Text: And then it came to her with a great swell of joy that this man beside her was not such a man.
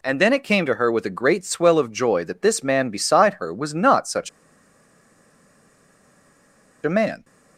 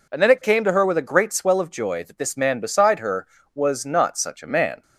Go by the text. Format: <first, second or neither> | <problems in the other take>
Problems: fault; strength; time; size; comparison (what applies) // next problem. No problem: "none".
second | pauses between "such" and "a"; strong; at 4.2 s; 2.5 s long